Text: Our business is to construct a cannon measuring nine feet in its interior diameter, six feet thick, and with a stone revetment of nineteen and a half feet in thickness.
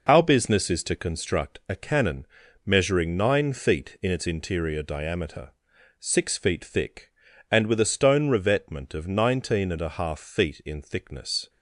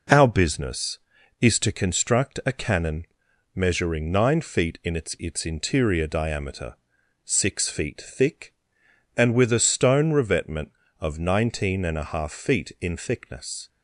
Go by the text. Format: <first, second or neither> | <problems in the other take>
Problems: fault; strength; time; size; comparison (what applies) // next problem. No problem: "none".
first | pauses between "cannon" and "measuring"; noticeable; at 3.0 s; 0.50 s long; also in the first // says "its" twice; at 5.1 s